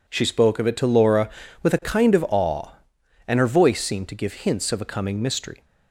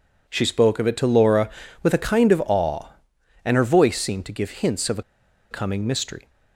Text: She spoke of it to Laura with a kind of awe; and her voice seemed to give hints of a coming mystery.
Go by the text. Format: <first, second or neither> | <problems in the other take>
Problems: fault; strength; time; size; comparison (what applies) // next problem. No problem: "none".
first | pauses between "a" and "coming"; noticeable; at 5.0 s; 0.47 s long